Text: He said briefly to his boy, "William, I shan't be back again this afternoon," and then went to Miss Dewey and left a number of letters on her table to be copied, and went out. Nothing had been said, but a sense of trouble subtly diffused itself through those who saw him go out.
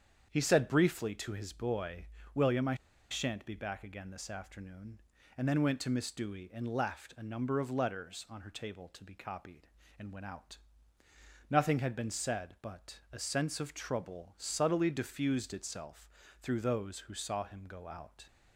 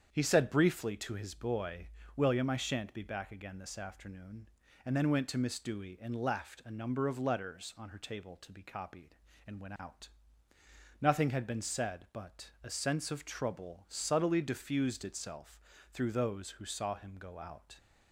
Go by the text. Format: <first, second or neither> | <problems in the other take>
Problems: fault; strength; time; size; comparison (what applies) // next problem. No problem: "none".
second | starts louder than the rest; strong; until 1.3 s; 8 dB; strong in the second // pauses between "I" and "shan't"; at 2.7 s; 0.36 s long // pauses between "itself" and "through"; slight; at 16.0 s; 0.32 s long; slight in the second